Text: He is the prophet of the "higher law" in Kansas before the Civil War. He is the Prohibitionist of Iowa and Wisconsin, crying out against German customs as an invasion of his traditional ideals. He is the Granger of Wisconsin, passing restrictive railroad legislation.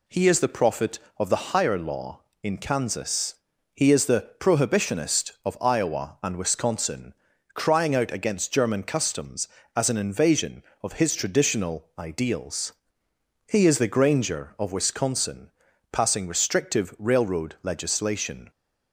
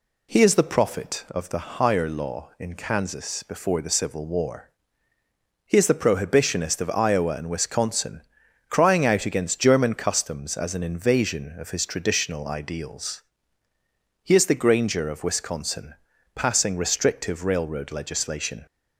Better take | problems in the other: second | skips "before the Civil War"; at 3.5 s

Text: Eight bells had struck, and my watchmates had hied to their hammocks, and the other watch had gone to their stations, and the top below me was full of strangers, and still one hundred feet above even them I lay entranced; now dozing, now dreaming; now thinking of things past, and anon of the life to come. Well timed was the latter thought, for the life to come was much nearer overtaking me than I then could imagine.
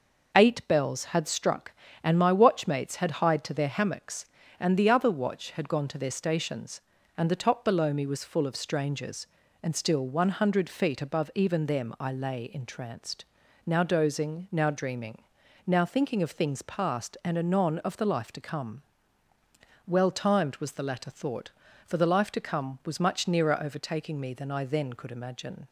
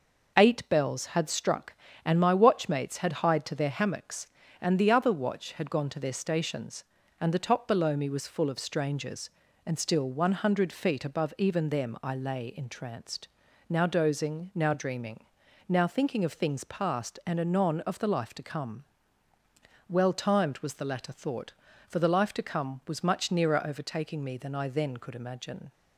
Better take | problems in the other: neither | none

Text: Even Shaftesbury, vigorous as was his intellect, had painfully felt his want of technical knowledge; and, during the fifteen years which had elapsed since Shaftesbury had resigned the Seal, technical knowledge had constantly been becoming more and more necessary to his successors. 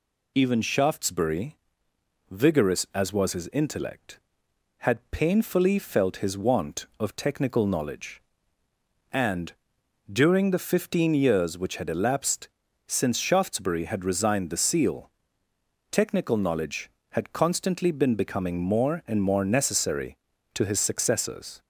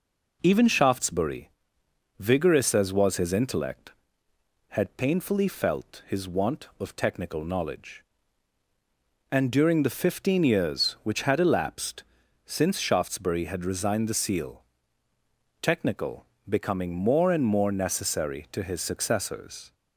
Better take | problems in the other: first | pauses between "elapsed" and "since"; at 12.0 s; 0.42 s long; also in the first // skips "knowledge had constantly been"; at 16.3 s

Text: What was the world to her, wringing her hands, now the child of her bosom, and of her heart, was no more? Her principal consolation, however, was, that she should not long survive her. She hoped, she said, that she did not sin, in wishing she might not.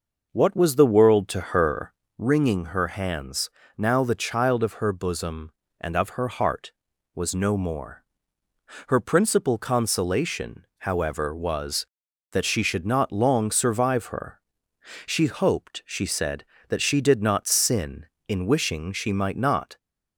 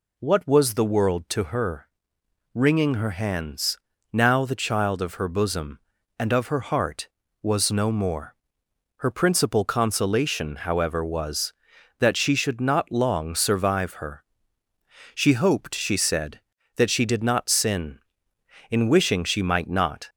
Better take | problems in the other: second | starts louder than the rest; noticeable; until 2.1 s; 5.5 dB

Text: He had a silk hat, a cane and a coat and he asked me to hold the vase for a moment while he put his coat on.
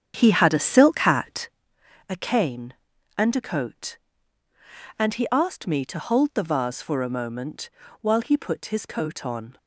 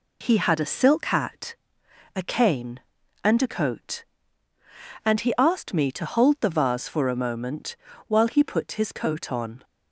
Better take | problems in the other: second | starts louder than the rest; strong; until 1.6 s; 8.5 dB // pauses between "moment" and "while"; slight; at 7.6 s; 0.30 s long; slight in the second

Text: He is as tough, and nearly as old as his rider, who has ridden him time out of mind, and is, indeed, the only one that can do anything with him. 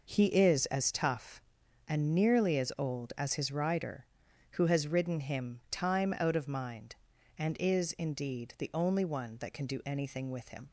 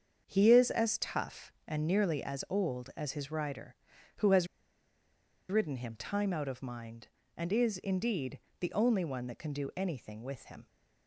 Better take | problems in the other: first | starts louder than the rest; until 1.2 s; 7 dB // pauses between "has" and "ridden"; at 4.4 s; 1.0 s long

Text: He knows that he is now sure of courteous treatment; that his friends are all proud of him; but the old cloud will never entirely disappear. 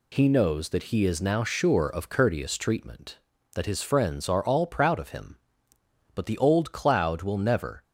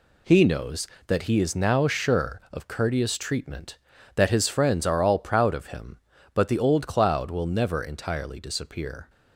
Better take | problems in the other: second | stops before "entirely disappear"; at 7.8 s

